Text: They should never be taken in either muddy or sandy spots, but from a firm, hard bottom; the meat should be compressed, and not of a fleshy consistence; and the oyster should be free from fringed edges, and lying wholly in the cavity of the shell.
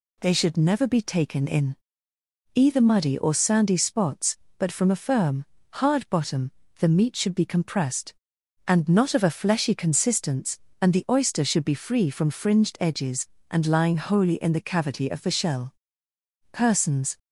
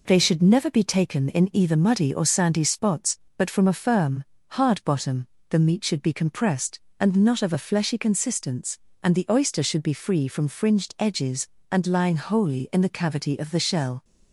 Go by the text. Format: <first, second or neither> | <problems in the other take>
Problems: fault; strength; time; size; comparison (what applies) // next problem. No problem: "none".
second | pauses between "in" and "either"; noticeable; at 1.7 s; 0.78 s long // goes on to say "Persons"; noticeable; from 16.5 s on; 0.66 s long